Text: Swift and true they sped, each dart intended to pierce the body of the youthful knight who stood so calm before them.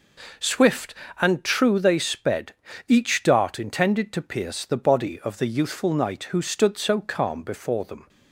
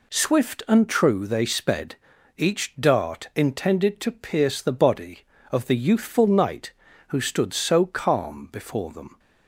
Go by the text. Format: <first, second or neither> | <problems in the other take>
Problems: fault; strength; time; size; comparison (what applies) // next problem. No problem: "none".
neither | none